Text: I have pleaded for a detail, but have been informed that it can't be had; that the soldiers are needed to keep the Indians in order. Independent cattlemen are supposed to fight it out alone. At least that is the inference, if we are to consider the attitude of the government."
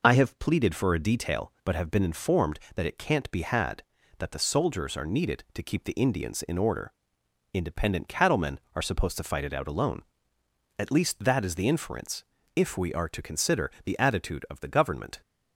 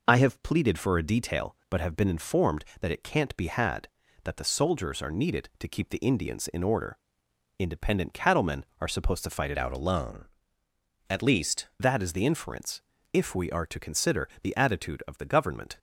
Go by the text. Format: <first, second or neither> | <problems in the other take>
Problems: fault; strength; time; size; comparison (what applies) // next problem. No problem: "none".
first | changes voice from "out" to "least"; from 9.5 to 11.6 s; 2.1 s long